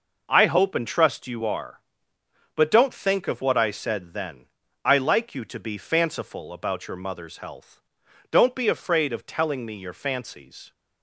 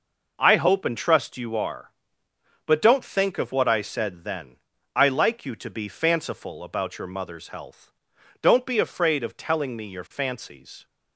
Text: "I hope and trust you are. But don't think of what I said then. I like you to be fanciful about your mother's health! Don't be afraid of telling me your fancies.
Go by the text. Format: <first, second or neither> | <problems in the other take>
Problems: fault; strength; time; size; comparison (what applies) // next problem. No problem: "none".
neither | none